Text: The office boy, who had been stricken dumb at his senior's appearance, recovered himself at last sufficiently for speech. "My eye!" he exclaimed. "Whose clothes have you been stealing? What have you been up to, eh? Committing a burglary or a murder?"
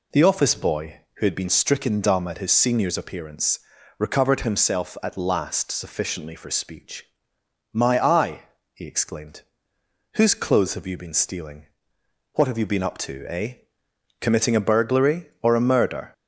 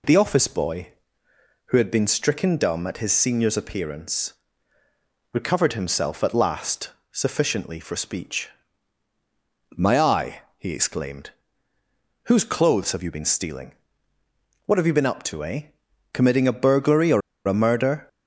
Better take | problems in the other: first | pauses between "last" and "sufficiently"; slight; at 6.9 s; 0.20 s long // pauses between "or" and "a"; slight; at 17.2 s; 0.27 s long

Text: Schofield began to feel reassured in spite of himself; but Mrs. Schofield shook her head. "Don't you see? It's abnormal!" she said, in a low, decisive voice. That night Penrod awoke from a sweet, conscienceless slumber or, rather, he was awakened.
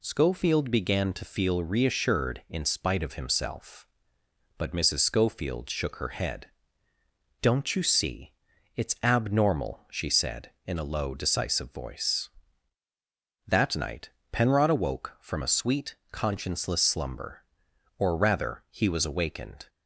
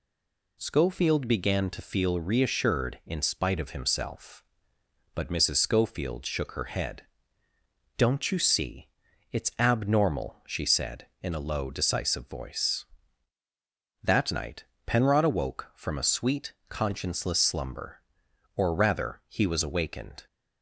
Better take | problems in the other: first | stays silent before the first word; slight; until 0.5 s; 0.5 s long // pauses between "night" and "Penrod"; slight; at 14.6 s; 0.22 s long; slight in the first

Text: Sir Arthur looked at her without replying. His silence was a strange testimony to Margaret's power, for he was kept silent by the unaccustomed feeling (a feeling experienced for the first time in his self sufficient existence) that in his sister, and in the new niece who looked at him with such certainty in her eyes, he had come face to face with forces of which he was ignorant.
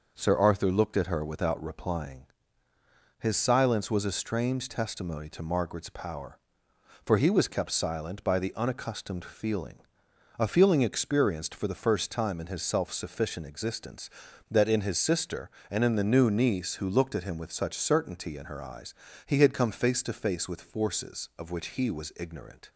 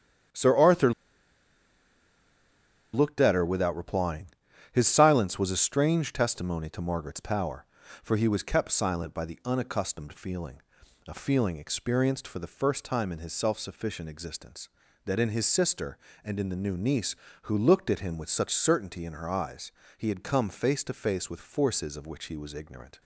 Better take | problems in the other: first | starts louder than the rest; strong; until 3.3 s; 9.5 dB // pauses between "Arthur" and "looked"; strong; at 0.9 s; 2.0 s long

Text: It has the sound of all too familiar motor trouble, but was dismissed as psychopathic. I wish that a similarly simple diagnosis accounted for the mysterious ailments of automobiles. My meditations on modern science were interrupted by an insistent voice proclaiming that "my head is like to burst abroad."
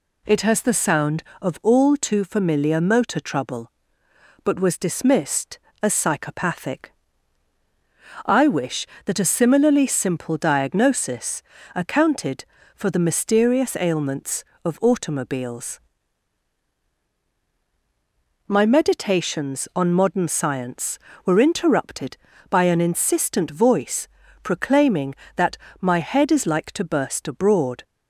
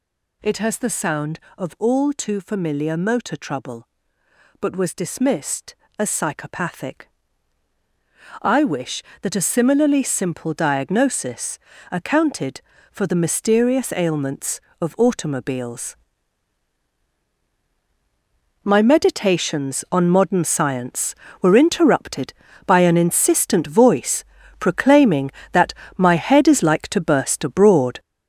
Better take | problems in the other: first | gets louder; strong; throughout; 7 dB // pauses between "diagnosis" and "accounted"; slight; at 11.5 s; 0.32 s long; slight in the first // pauses between "voice" and "proclaiming"; slight; at 24.2 s; 0.34 s long; slight in the first // pauses between "that" and "my"; slight; at 25.7 s; 0.22 s long; slight in the first

